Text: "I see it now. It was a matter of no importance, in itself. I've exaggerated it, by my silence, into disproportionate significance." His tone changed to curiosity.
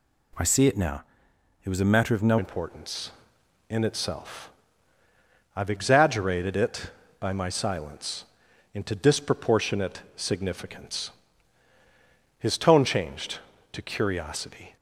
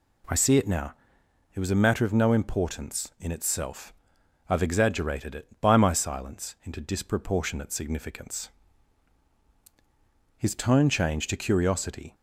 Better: second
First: changes voice at "importance"; from 2.3 s on; 12.4 s long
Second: none

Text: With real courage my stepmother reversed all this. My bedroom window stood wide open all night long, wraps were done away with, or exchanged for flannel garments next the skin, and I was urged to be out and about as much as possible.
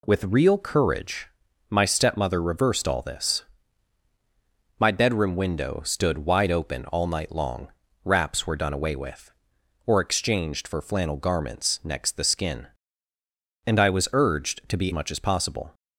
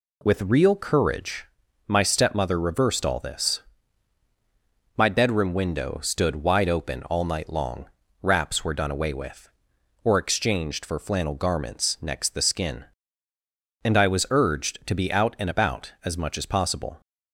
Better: second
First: pauses between "courage" and "my"; at 1.2 s; 0.42 s long // skips "out and about as"; at 14.9 s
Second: pauses between "courage" and "my"; at 1.4 s; 0.42 s long

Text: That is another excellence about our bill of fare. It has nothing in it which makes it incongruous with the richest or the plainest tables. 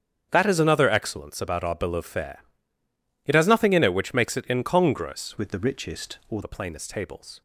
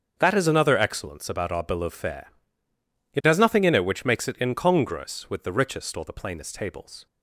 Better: second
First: starts louder than the rest; strong; until 1.3 s; 7.5 dB // changes voice from "with" to "or"; from 5.3 to 6.4 s; 1.1 s long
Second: starts louder than the rest; until 1.1 s; 6.5 dB

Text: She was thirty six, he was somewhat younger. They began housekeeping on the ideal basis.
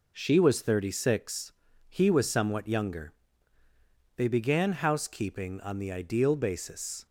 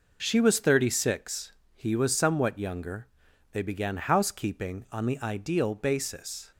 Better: neither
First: none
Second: none

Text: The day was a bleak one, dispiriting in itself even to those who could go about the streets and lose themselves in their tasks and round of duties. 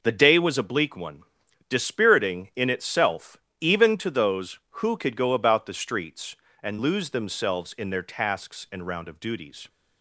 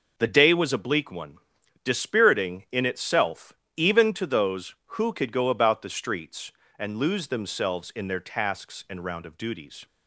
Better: neither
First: pauses between "itself" and "even"; slight; at 3.3 s; 0.24 s long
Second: pauses between "itself" and "even"; slight; at 3.5 s; 0.24 s long

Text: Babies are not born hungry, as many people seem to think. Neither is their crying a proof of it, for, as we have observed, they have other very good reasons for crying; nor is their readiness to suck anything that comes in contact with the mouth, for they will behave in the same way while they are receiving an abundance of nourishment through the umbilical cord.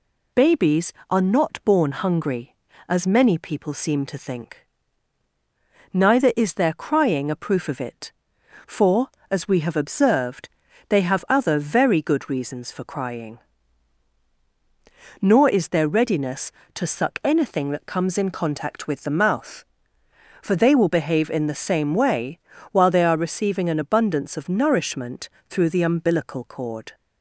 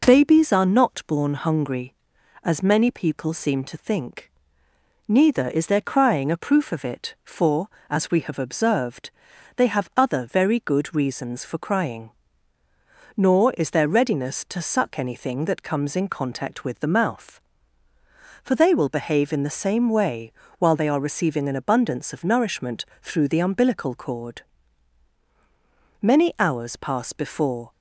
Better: first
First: pauses between "way" and "while"; slight; at 22.3 s; 0.32 s long // pauses between "nourishment" and "through"; slight; at 25.2 s; 0.20 s long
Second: pauses between "way" and "while"; slight; at 20.3 s; 0.24 s long // pauses between "nourishment" and "through"; slight; at 22.8 s; 0.18 s long // goes on to say "Many hours pass before"; strong; from 26.0 s on; 1.7 s long

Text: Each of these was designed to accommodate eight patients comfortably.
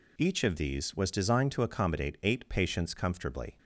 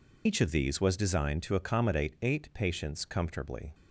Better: first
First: none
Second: loses the start of "Each"; at 0.2 s; 50 ms

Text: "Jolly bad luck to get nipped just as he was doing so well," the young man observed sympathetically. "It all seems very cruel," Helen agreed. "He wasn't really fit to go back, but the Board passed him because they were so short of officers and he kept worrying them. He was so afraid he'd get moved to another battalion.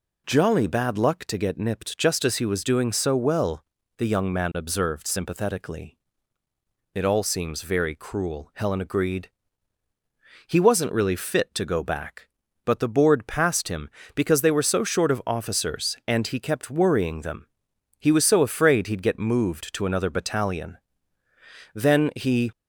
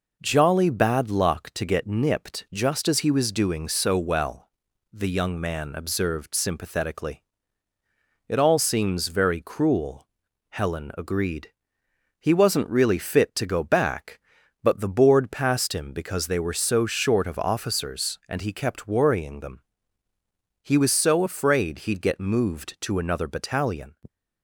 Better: second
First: goes on to say "Then he"; noticeable; from 21.7 s on; 0.78 s long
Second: none

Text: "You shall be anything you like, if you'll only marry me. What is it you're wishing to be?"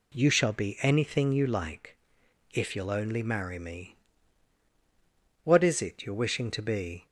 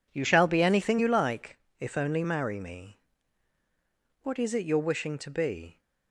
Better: first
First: none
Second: skips "you'll"; at 1.9 s

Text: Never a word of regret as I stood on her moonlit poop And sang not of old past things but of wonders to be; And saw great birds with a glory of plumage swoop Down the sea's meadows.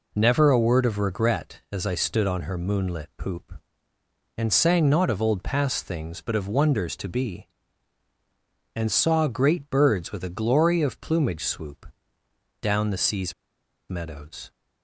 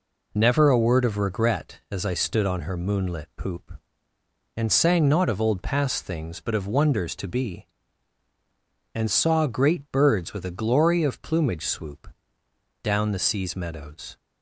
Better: second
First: pauses between "swoop" and "Down"; noticeable; at 11.9 s; 0.70 s long // pauses between "sea's" and "meadows"; noticeable; at 13.3 s; 0.56 s long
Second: pauses between "swoop" and "Down"; noticeable; at 12.1 s; 0.70 s long

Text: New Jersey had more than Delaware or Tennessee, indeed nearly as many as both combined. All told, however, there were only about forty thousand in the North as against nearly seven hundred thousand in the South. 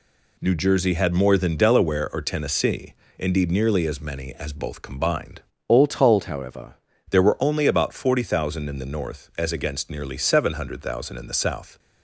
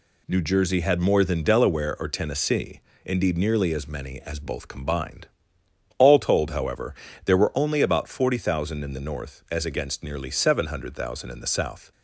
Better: second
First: changes voice from "All" to "however"; from 5.6 to 6.7 s; 1.1 s long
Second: none

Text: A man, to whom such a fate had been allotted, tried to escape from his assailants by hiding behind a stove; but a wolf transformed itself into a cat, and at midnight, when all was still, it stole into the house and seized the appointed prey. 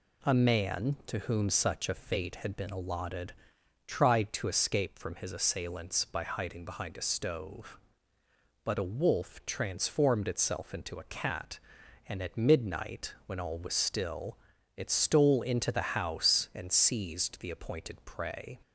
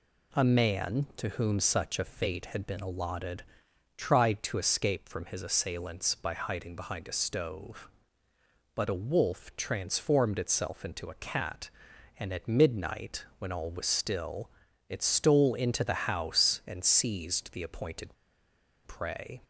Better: first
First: none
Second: pauses between "appointed" and "prey"; noticeable; at 18.1 s; 0.70 s long

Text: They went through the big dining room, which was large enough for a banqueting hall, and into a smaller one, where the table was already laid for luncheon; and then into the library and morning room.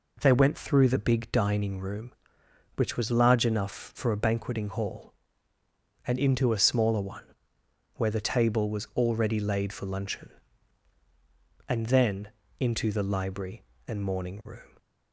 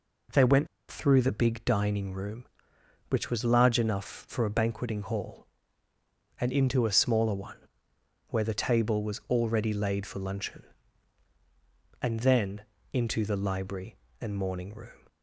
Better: first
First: pauses between "then" and "into"; slight; at 12.2 s; 0.30 s long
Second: pauses between "went" and "through"; slight; at 0.6 s; 0.24 s long // pauses between "then" and "into"; slight; at 12.6 s; 0.30 s long

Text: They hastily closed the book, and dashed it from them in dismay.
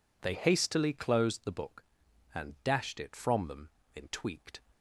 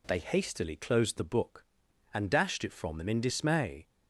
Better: second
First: says "tweaked" for "dismay"; at 4.0 s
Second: none

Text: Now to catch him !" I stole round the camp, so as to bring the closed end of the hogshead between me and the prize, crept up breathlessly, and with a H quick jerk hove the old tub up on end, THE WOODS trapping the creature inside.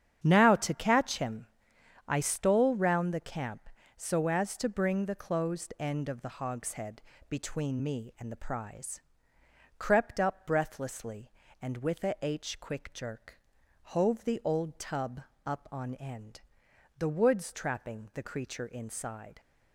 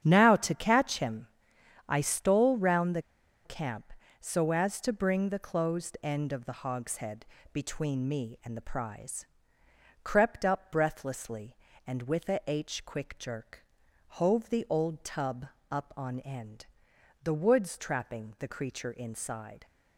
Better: first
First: starts louder than the rest; strong; until 1.2 s; 9 dB // pauses between "hogshead" and "between"; slight; at 7.0 s; 0.26 s long // pauses between "jerk" and "hove"; at 13.3 s; 0.42 s long // pauses between "tub" and "up"; slight; at 15.2 s; 0.24 s long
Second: starts louder than the rest; strong; until 1.0 s; 9 dB // pauses between "the" and "camp"; at 3.0 s; 0.43 s long // pauses between "hogshead" and "between"; slight; at 7.2 s; 0.26 s long // pauses between "jerk" and "hove"; at 13.6 s; 0.42 s long // pauses between "tub" and "up"; slight; at 15.4 s; 0.24 s long

